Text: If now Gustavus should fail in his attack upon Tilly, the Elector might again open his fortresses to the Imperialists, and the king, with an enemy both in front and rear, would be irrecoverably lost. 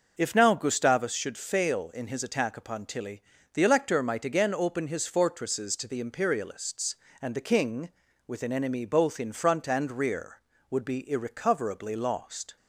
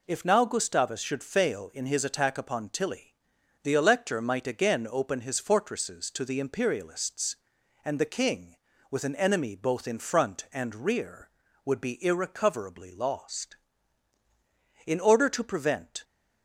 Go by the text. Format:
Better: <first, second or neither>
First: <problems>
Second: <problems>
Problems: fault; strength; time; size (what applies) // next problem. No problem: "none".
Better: first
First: none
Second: goes on to say "In order to prevent"; noticeable; from 14.8 s on; 1.1 s long